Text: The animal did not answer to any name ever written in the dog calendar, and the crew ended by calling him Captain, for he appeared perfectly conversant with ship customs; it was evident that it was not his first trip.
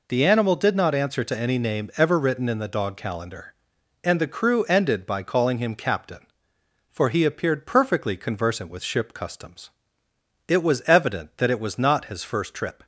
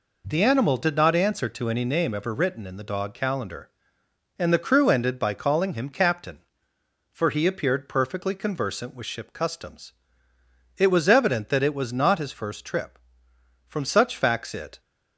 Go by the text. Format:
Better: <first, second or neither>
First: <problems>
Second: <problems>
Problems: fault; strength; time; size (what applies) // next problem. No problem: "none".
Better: first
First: none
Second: goes on to say "From such facts it"; noticeable; from 13.6 s on; 1.1 s long